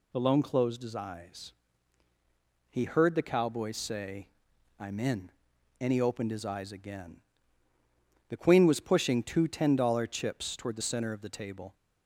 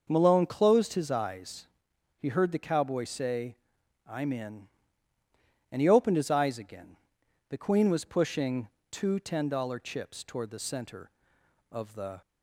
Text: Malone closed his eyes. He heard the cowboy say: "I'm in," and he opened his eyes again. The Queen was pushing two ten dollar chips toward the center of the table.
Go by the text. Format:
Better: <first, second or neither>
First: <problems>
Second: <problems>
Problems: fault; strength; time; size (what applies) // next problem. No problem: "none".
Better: first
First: none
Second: starts louder than the rest; noticeable; until 1.0 s; 6 dB // pauses between "pushing" and "two"; slight; at 8.6 s; 0.20 s long // stops before "table"; at 12.2 s